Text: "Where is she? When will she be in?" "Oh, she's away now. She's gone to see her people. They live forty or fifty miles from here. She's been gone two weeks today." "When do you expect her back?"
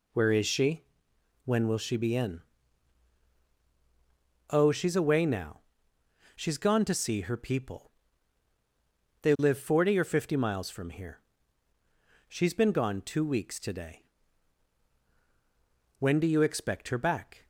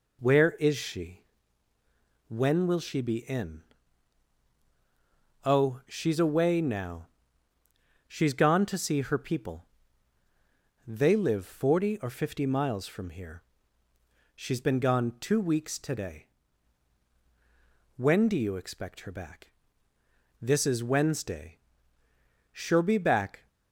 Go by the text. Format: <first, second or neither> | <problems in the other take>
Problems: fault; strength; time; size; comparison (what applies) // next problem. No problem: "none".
first | goes on to say "This is Wednesday She'll be back"; strong; from 20.4 s on; 3.0 s long